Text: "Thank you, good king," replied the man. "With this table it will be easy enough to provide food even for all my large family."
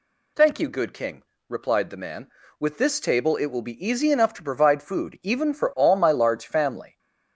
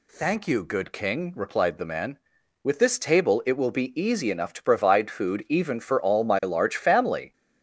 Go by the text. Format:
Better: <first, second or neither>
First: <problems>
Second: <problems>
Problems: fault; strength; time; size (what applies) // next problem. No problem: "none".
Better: neither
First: none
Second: none